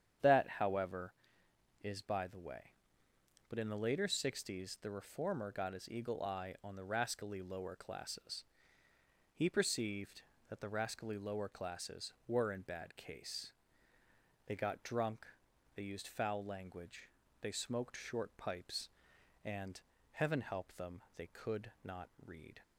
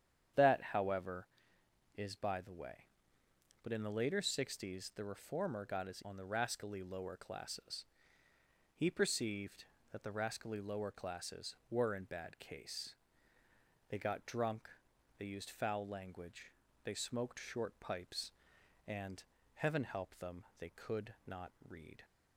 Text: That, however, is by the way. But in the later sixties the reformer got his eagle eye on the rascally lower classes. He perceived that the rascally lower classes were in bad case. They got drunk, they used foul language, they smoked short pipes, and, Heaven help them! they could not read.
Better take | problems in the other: first | starts louder than the rest; strong; until 2.1 s; 8.5 dB; strong in the first // skips "eagle eye"; at 6.0 s // pauses between "not" and "read"; slight; at 21.5 s; 0.16 s long; slight in the first

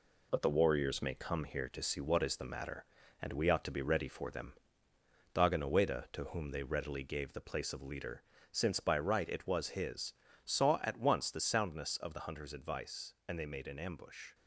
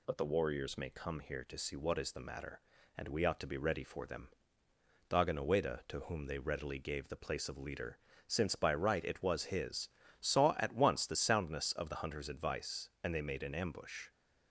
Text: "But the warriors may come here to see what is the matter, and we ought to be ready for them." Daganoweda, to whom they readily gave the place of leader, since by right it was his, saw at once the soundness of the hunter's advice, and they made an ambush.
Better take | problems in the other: second | gets quieter; noticeable; throughout; 4.5 dB

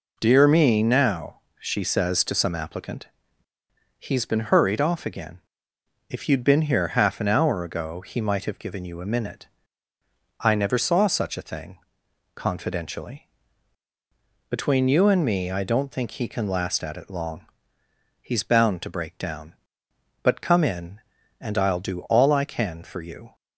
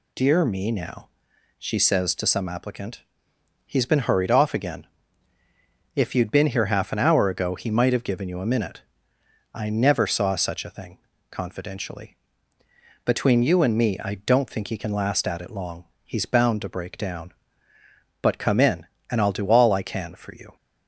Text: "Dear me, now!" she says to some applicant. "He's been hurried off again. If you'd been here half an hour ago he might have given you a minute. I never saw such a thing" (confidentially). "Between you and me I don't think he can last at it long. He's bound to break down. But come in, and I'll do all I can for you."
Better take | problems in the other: neither | none

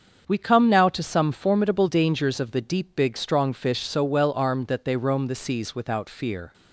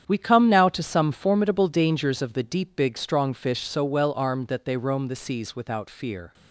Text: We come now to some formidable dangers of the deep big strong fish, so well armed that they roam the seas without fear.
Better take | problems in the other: first | gets quieter; strong; throughout; 10.5 dB // starts louder than the rest; strong; until 1.0 s; 8.5 dB; also in the first

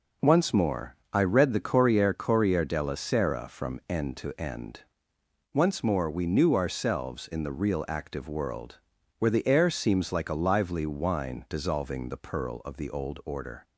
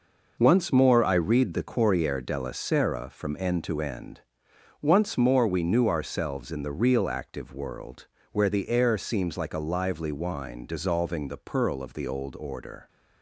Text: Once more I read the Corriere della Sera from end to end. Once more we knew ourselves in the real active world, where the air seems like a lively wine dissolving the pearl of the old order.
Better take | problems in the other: second | pauses between "more" and "I"; slight; at 0.9 s; 0.18 s long // says "Corriere" twice; at 2.1 s

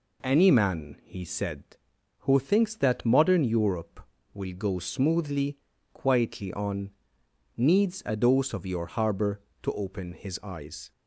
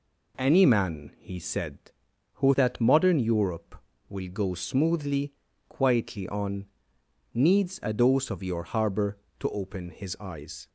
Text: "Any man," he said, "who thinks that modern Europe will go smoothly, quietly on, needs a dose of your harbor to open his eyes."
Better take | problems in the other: first | skips "thinks"; at 2.5 s

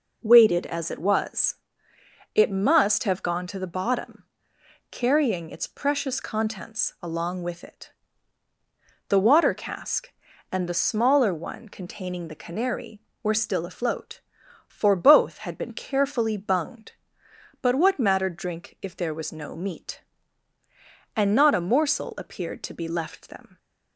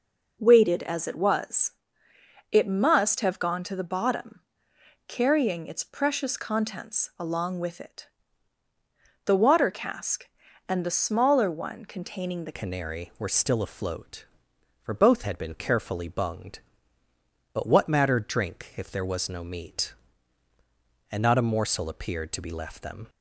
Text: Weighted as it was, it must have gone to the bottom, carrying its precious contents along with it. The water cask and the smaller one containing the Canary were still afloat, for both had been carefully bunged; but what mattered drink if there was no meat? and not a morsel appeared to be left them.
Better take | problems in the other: first | changes voice at "Canary"; from 12.5 s on; 10.5 s long

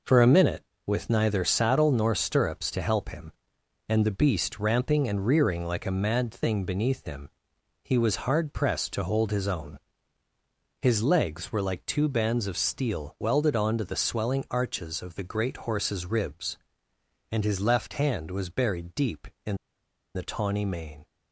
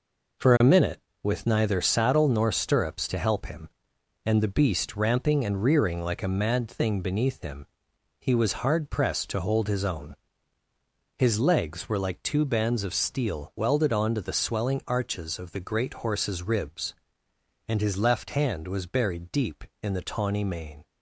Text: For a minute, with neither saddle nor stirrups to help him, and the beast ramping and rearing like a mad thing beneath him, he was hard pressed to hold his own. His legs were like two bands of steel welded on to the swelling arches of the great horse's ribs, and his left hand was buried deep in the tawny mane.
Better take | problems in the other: second | pauses between "in" and "the"; noticeable; at 19.5 s; 0.60 s long

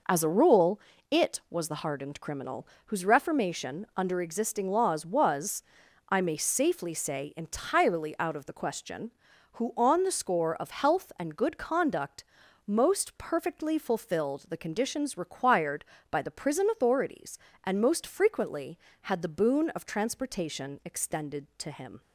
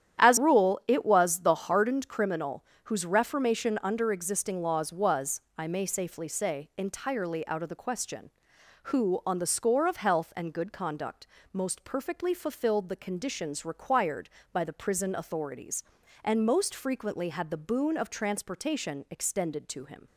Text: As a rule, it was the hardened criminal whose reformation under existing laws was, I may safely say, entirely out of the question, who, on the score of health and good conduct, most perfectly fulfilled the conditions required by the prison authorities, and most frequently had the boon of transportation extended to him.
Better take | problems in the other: first | starts louder than the rest; strong; until 1.2 s; 10.5 dB // skips "a"; at 0.3 s // pauses between "criminal" and "whose"; slight; at 2.6 s; 0.20 s long; slight in the first

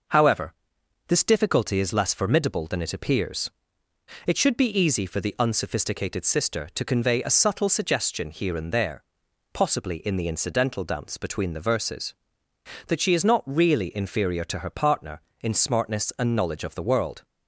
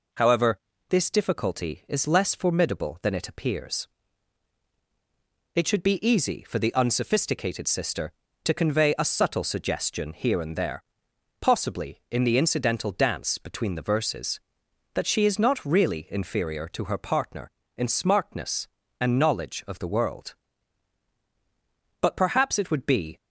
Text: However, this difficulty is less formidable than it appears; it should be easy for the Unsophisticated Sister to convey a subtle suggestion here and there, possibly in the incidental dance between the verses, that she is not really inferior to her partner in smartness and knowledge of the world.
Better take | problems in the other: first | goes on to say "But perhaps it would be"; noticeable; from 22.0 s on; 1.1 s long

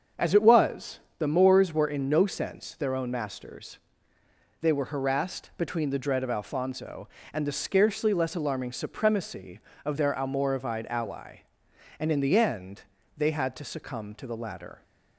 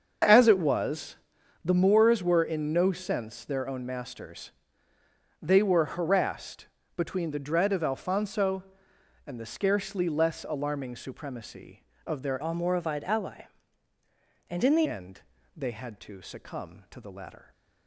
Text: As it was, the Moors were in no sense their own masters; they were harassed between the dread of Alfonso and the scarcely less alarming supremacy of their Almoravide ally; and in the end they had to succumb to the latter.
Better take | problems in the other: first | starts louder than the rest; until 1.7 s; 6.5 dB; also in the first // pauses between "harassed" and "between"; slight; at 6.6 s; 0.28 s long // changes voice from "Almoravide" to "the"; from 12.4 to 14.8 s; 2.4 s long // pauses between "end" and "they"; slight; at 15.2 s; 0.34 s long; slight in the first

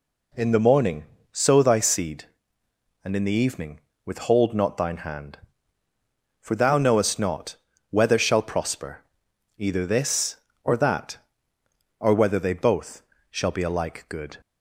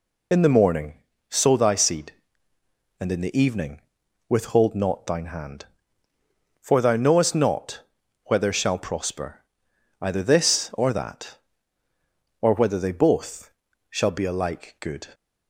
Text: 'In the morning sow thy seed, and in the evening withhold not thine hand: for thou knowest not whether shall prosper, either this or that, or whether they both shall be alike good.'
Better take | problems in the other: first | loses the start of "In"; at 0.3 s; 50 ms // pauses between "morning" and "sow"; slight; at 0.9 s; 0.34 s long; slight in the first // pauses between "evening" and "withhold"; noticeable; at 3.7 s; 0.48 s long; slight in the first // pauses between "not" and "whether"; at 7.8 s; 0.42 s long; slight in the first // pauses between "both" and "shall"; at 13.4 s; 0.40 s long; slight in the first

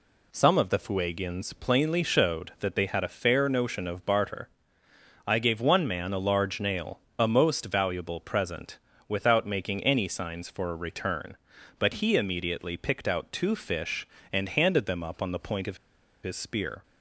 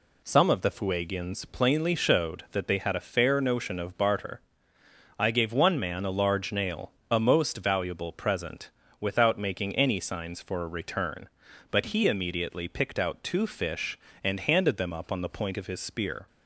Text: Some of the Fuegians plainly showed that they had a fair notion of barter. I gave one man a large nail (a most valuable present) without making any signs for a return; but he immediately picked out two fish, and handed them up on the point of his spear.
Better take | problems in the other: second | pauses between "of" and "his"; noticeable; at 15.7 s; 0.46 s long

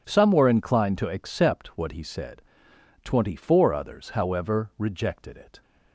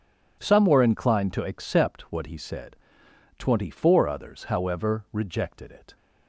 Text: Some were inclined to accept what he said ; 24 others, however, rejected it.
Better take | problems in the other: neither | none

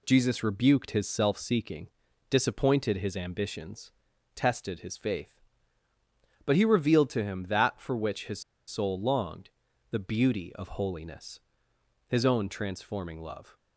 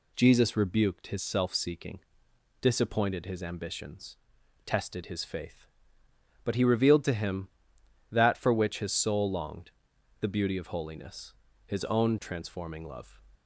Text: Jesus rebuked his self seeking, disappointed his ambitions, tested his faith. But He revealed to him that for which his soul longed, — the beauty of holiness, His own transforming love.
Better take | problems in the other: second | pauses between "his" and "soul"; slight; at 8.4 s; 0.26 s long

